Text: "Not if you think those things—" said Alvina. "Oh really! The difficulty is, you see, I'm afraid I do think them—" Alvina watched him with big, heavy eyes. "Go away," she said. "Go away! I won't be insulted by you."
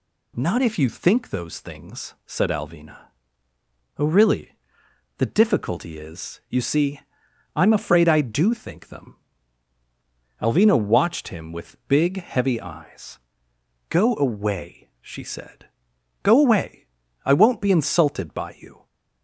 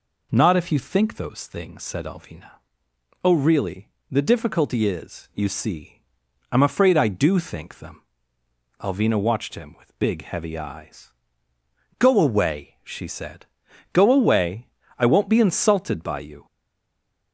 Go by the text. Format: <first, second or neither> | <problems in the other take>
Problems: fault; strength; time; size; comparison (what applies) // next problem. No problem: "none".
first | stays silent after the last word; slight; from 16.4 s on; 0.9 s long